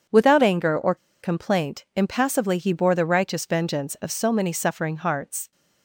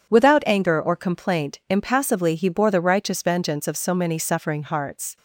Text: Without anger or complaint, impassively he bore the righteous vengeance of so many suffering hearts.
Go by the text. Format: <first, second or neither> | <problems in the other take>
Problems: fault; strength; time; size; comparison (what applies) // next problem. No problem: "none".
second | starts louder than the rest; strong; until 1.3 s; 7.5 dB // pauses between "or" and "complaint"; slight; at 0.9 s; 0.26 s long